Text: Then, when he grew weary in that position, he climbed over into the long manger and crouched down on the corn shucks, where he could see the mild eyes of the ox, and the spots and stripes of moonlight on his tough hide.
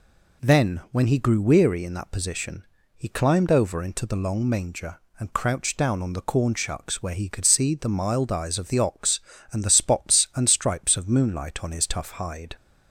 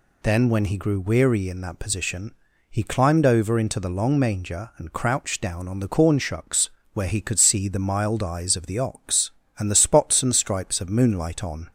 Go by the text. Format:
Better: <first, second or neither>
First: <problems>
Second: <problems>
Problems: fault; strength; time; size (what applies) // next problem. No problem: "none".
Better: first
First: none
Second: stops before "his tough hide"; at 11.6 s